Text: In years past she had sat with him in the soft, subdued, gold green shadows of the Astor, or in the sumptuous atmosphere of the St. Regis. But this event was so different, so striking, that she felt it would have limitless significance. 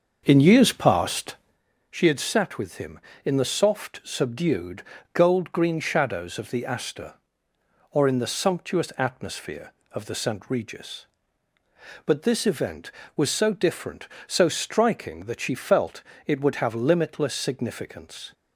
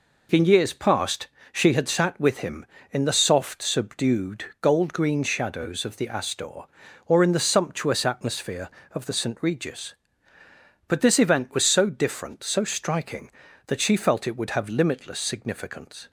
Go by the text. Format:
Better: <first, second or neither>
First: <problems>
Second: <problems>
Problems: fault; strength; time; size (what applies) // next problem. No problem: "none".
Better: second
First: starts louder than the rest; until 1.6 s; 6.5 dB // pauses between "past" and "she"; noticeable; at 1.3 s; 0.56 s long // pauses between "felt" and "it"; slight; at 16.0 s; 0.24 s long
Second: pauses between "past" and "she"; slight; at 1.2 s; 0.26 s long